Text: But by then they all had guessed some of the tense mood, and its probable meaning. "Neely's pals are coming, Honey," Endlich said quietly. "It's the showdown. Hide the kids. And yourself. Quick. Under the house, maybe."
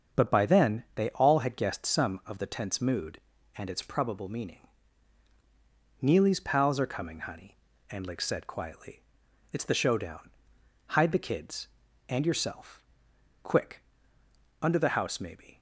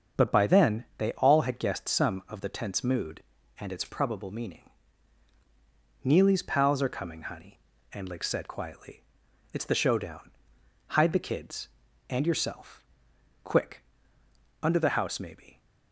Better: neither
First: starts louder than the rest; until 1.2 s; 6.5 dB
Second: starts louder than the rest; until 1.3 s; 6.5 dB

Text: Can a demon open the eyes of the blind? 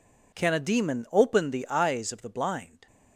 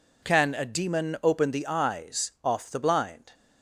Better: first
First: none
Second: says "off" for "of"; at 2.4 s

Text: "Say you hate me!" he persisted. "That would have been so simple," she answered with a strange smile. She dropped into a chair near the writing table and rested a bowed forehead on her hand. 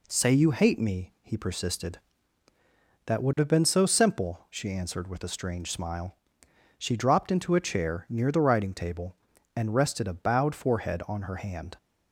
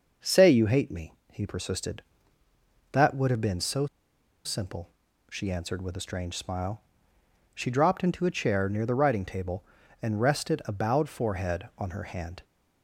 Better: first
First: none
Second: pauses between "so" and "simple"; noticeable; at 3.8 s; 0.58 s long

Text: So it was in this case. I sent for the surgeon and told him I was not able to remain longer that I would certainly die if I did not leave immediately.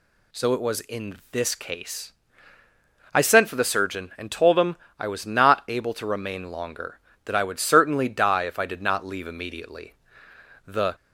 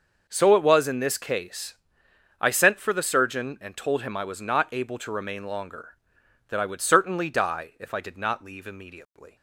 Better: second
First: pauses between "him" and "I"; slight; at 4.7 s; 0.22 s long // goes on to say "The"; slight; from 10.6 s on; 0.28 s long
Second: none

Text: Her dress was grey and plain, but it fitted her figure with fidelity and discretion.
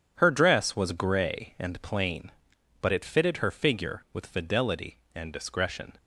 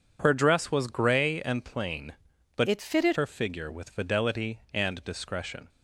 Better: first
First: none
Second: changes voice from "it" to "fitted"; from 2.6 to 3.1 s; 0.5 s long

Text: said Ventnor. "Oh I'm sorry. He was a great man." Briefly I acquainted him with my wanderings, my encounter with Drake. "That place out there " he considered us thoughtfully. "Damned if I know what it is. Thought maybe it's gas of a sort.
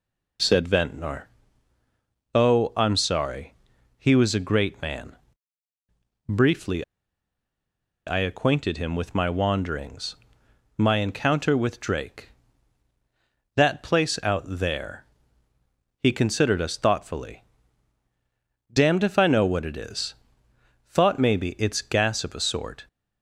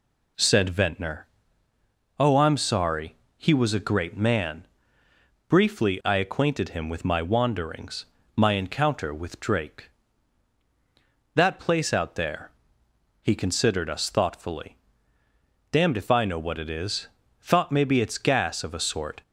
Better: second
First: pauses between "Briefly" and "I"; at 6.8 s; 1.2 s long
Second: none

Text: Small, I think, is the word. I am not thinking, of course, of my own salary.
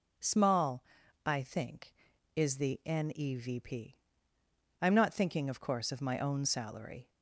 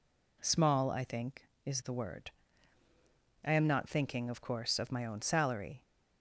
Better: second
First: says "nevp" for "word"; at 2.8 s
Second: none

